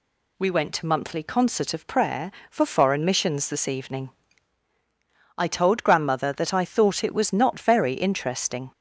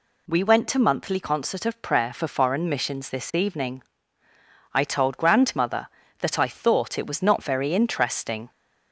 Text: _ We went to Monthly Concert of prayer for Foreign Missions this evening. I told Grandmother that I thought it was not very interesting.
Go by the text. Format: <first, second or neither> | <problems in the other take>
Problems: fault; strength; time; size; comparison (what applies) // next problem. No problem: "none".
neither | none